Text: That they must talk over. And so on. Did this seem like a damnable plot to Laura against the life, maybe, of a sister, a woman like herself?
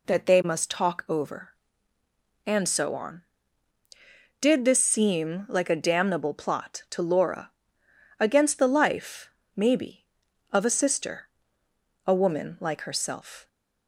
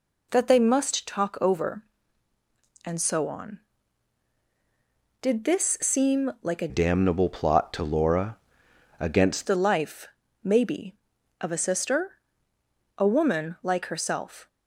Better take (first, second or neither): first